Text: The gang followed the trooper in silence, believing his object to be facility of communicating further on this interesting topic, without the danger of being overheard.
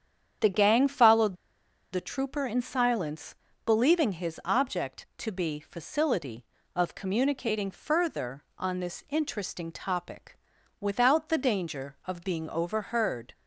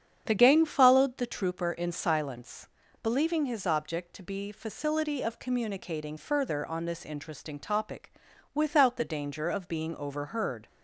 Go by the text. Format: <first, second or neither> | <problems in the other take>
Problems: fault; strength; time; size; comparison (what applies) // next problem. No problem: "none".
second | starts louder than the rest; strong; until 2.0 s; 8.5 dB; strong in the second // pauses between "followed" and "the"; noticeable; at 1.3 s; 0.57 s long